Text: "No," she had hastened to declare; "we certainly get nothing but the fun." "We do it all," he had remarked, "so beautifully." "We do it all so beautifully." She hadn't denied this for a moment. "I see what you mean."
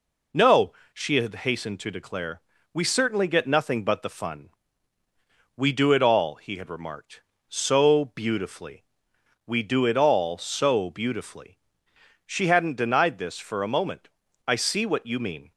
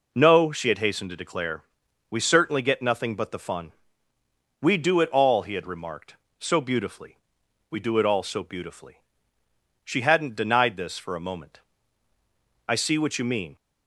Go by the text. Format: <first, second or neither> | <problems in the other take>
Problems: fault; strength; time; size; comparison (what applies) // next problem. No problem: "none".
neither | none